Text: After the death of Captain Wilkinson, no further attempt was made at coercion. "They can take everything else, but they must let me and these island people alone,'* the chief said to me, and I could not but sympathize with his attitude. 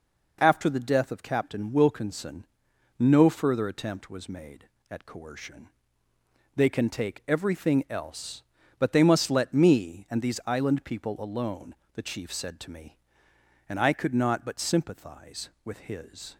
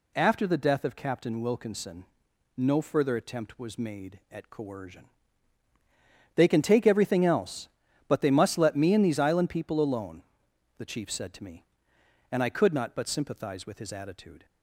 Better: second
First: stops before "attitude"; at 16.3 s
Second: none

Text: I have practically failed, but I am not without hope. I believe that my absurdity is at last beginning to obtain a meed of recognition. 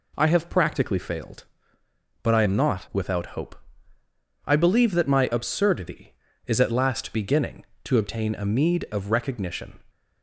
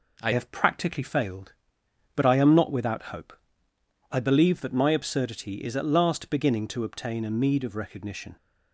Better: first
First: none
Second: changes voice at "have"; from 0.3 s on; 8.0 s long

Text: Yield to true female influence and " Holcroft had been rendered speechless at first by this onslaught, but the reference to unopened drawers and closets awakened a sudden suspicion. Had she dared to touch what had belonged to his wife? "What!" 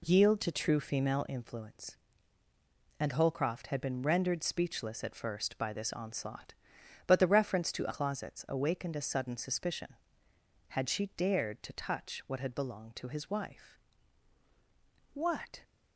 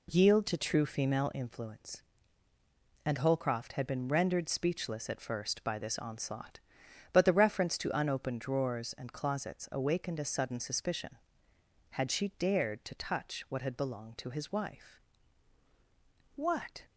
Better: second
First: skips "unopened drawers and"; at 7.9 s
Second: none

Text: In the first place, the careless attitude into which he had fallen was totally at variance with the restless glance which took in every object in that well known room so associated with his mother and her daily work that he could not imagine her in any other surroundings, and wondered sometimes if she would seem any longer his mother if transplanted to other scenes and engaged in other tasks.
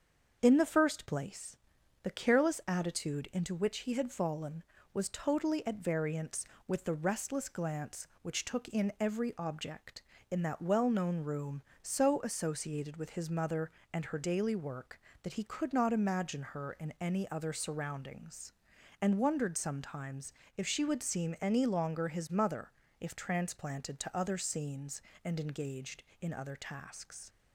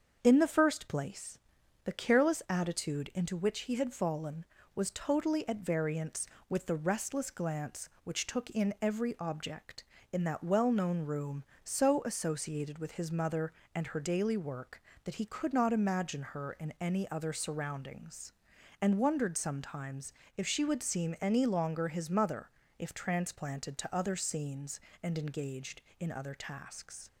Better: neither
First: starts louder than the rest; until 1.4 s; 7 dB // pauses between "sometimes" and "if"; slight; at 20.3 s; 0.24 s long // pauses between "mother" and "if"; slight; at 22.7 s; 0.28 s long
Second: starts louder than the rest; until 1.2 s; 7 dB // pauses between "sometimes" and "if"; slight; at 20.1 s; 0.24 s long // pauses between "mother" and "if"; slight; at 22.4 s; 0.28 s long

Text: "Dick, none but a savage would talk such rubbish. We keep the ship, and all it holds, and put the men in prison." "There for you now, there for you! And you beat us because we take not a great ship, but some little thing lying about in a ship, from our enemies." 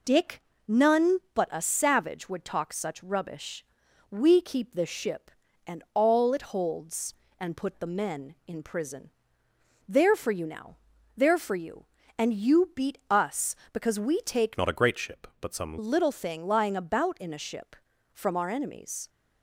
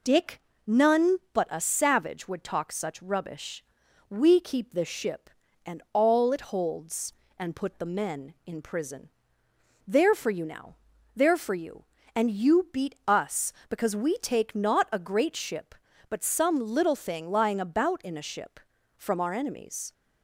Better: second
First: changes voice from "not" to "some"; from 14.5 to 15.7 s; 1.2 s long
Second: none

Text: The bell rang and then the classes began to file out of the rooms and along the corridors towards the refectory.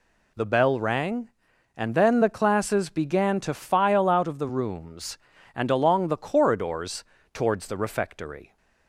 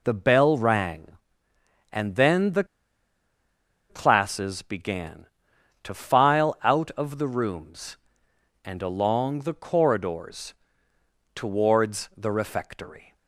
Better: first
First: pauses between "corridors" and "towards"; slight; at 7.0 s; 0.28 s long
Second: pauses between "the" and "classes"; strong; at 2.6 s; 1.2 s long // pauses between "corridors" and "towards"; noticeable; at 10.5 s; 0.80 s long

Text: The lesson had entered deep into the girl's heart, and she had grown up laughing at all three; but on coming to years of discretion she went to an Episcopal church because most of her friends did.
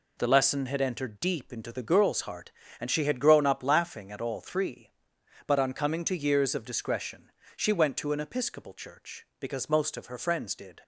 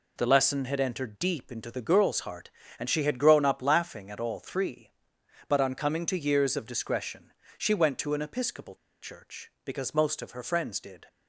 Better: first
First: pauses between "discretion" and "she"; slight; at 7.3 s; 0.24 s long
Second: pauses between "discretion" and "she"; slight; at 7.3 s; 0.24 s long // pauses between "Episcopal" and "church"; slight; at 8.7 s; 0.24 s long

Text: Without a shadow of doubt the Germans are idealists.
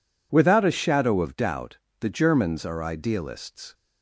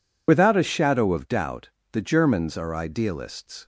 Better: first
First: pauses between "doubt" and "the"; slight; at 1.7 s; 0.24 s long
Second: loses the start of "Without"; at 0.2 s; 50 ms // pauses between "doubt" and "the"; slight; at 1.6 s; 0.24 s long

